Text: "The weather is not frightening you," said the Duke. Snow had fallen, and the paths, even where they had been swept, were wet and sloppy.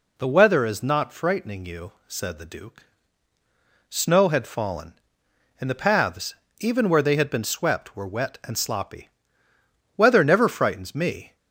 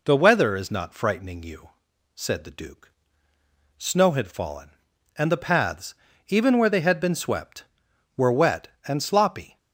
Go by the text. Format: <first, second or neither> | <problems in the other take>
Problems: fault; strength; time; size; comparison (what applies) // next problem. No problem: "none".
second | goes on to say "Weather never frightens me"; from 9.9 s on; 1.4 s long